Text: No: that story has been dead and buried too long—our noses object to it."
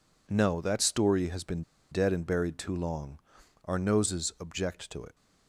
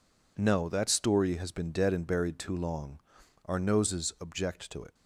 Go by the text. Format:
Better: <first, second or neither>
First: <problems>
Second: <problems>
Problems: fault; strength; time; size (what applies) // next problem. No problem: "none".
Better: second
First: pauses between "been" and "dead"; slight; at 1.6 s; 0.29 s long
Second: none